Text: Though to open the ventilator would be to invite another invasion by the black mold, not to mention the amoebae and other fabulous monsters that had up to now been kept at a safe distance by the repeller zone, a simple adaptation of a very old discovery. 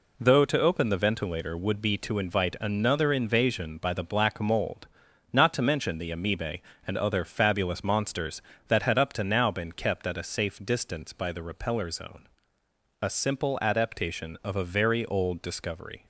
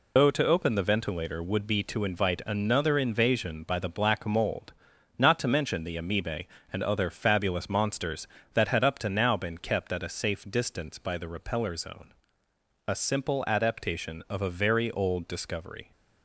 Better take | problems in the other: first | loses the start of "Though"; at 0.1 s; 130 ms

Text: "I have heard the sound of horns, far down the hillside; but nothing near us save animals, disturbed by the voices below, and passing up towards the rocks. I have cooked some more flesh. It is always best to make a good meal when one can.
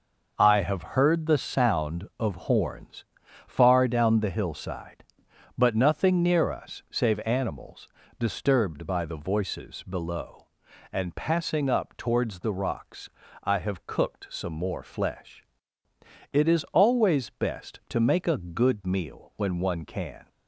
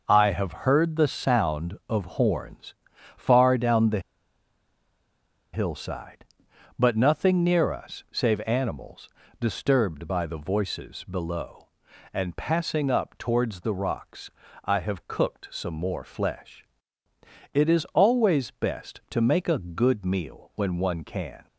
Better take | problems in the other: first | pauses between "the" and "hillside"; strong; at 3.9 s; 1.5 s long

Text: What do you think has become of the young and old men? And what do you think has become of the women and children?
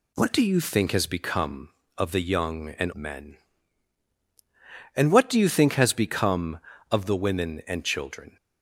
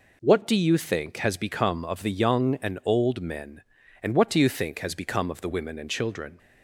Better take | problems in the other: second | skips "old"; at 2.9 s

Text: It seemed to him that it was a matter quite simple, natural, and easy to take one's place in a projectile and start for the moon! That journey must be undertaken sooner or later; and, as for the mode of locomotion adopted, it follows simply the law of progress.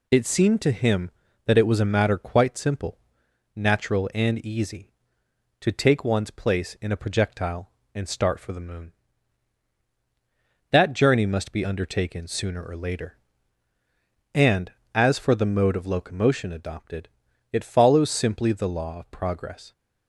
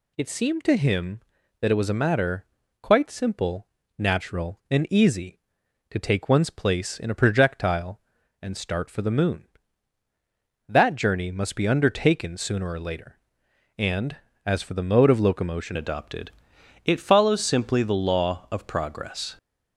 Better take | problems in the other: first | pauses between "matter" and "quite"; slight; at 2.4 s; 0.36 s long // changes voice at "adopted"; from 15.7 s on; 3.6 s long

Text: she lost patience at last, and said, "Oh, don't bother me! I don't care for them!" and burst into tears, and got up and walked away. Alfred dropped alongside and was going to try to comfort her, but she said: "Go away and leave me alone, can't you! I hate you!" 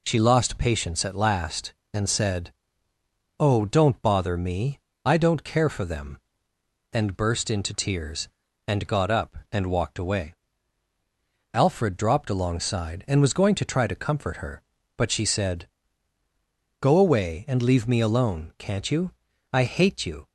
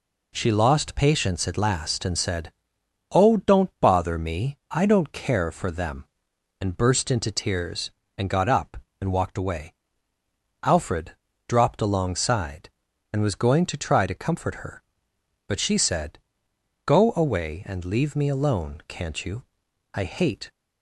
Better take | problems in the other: first | pauses between "Alfred" and "dropped"; slight; at 11.1 s; 0.36 s long // stops before "you"; at 20.4 s

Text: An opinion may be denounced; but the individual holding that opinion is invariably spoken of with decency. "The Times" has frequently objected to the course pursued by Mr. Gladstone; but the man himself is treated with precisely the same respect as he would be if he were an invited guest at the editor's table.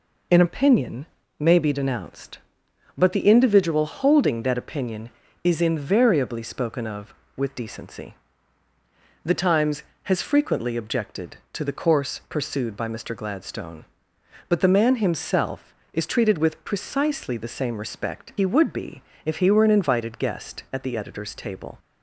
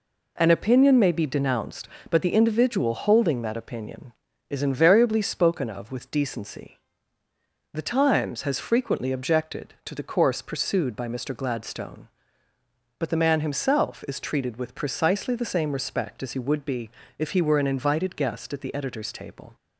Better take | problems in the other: second | pauses between "opinion" and "may"; slight; at 1.0 s; 0.32 s long // skips "as"; at 18.3 s // pauses between "be" and "if"; slight; at 19.0 s; 0.22 s long; slight in the second

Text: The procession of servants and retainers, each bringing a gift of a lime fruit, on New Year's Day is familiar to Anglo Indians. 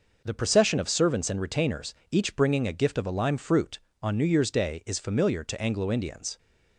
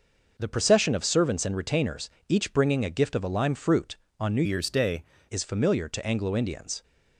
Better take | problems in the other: first | changes voice from "Year's" to "Day"; from 4.4 to 5.0 s; 0.6 s long

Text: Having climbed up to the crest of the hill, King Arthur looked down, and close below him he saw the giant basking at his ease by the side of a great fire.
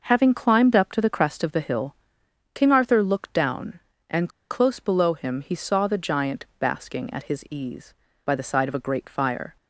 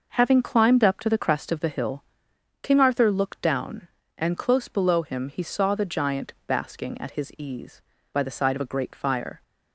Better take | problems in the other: second | pauses between "and" and "close"; slight; at 4.2 s; 0.21 s long

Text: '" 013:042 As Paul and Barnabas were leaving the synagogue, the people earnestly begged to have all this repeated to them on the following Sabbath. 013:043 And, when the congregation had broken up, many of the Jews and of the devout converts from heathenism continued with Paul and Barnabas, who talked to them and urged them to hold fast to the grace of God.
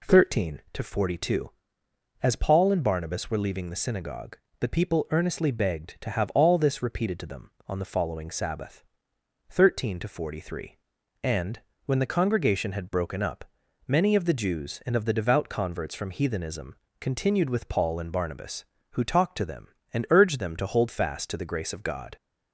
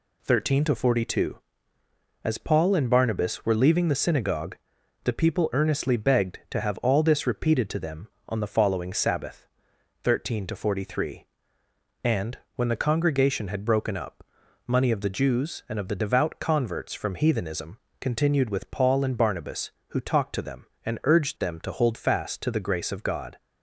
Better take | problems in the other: first | says "money" for "many"; at 14.6 s // pauses between "heathenism" and "continued"; slight; at 17.7 s; 0.20 s long; slight in the first

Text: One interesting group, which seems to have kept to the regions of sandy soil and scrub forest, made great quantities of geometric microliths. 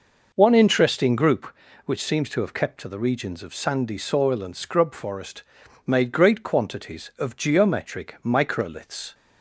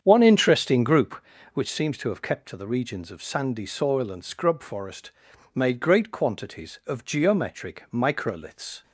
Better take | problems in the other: first | starts louder than the rest; strong; until 1.8 s; 8 dB

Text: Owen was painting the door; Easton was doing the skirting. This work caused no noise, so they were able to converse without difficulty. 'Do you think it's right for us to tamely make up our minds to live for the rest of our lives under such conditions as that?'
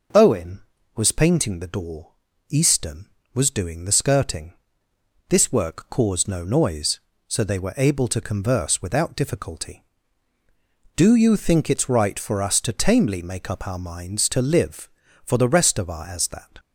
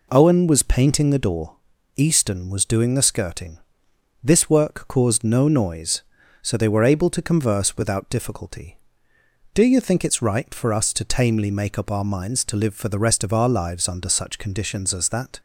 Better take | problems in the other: second | skips "lives under such conditions"; at 16.0 s

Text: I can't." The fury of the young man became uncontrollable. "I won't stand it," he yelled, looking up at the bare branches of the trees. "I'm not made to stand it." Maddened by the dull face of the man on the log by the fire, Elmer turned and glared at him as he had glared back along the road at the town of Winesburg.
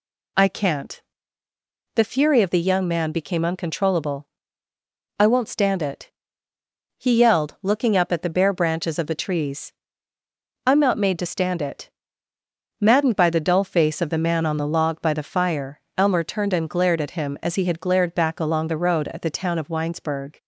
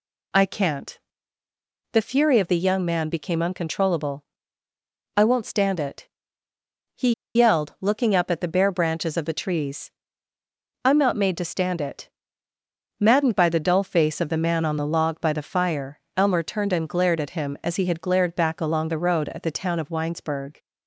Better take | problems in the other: first | pauses between "he" and "yelled"; slight; at 7.1 s; 0.21 s long

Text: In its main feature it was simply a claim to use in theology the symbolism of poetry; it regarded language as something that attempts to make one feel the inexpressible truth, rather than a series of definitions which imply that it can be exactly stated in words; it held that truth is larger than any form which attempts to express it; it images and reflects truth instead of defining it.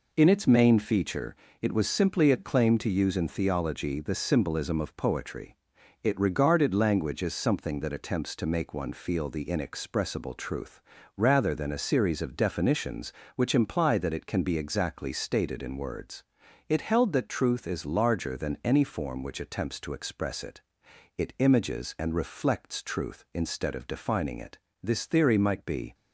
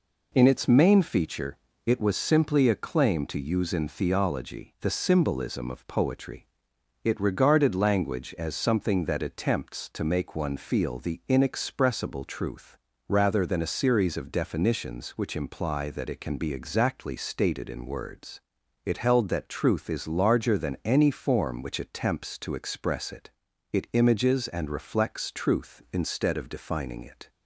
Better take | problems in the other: second | pauses between "feature" and "it"; slight; at 1.3 s; 0.26 s long; slight in the second // goes on to say "This theory might be"; noticeable; from 24.8 s on; 1.1 s long

